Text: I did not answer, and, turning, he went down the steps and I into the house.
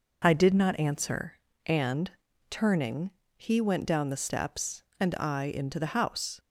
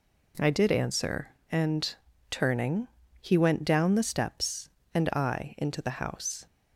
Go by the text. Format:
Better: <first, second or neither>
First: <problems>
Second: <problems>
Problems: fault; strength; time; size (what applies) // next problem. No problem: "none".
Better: first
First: none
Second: skips "not"; at 0.6 s